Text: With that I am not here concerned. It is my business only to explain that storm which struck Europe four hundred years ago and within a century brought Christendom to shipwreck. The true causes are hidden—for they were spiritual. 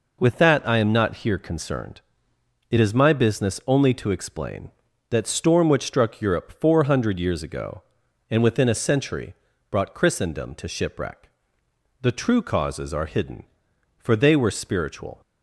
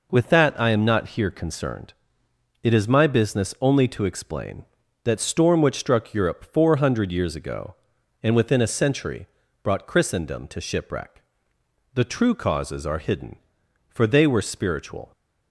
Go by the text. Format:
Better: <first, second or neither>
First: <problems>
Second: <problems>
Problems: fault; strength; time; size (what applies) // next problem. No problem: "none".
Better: neither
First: pauses between "century" and "brought"; slight; at 9.3 s; 0.34 s long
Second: pauses between "century" and "brought"; slight; at 9.2 s; 0.34 s long